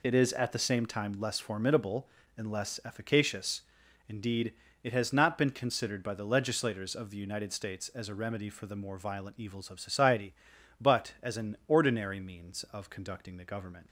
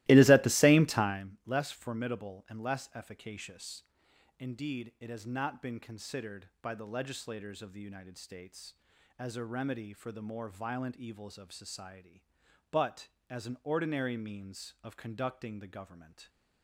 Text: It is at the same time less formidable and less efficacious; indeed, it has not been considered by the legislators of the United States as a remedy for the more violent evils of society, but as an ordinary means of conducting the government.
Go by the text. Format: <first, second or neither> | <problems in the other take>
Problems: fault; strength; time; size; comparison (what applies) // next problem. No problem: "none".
first | starts louder than the rest; strong; until 1.3 s; 18 dB